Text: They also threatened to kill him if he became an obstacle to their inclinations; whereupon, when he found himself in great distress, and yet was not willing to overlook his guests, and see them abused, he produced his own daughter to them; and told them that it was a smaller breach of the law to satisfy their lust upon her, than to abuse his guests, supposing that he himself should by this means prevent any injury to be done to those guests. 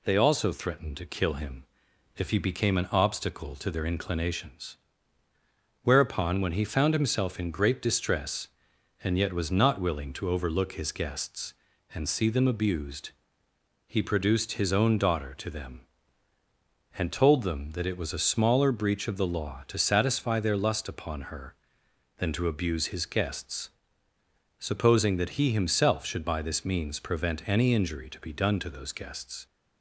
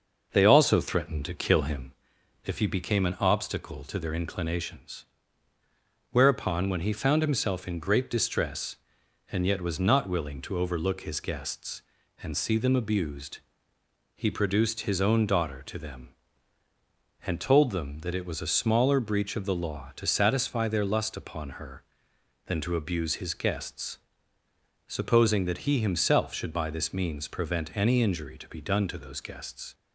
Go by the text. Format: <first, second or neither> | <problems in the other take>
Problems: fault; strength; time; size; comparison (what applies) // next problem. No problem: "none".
first | starts louder than the rest; noticeable; until 1.9 s; 6 dB // pauses between "him" and "if"; noticeable; at 1.9 s; 0.52 s long; noticeable in the first